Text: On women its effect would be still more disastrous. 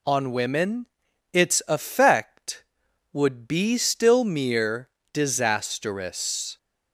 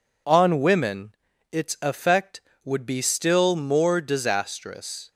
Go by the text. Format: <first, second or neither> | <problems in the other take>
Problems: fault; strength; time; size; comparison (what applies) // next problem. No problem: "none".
second | pauses between "women" and "its"; at 0.8 s; 0.44 s long; slight in the second // says "mere" for "more"; at 4.2 s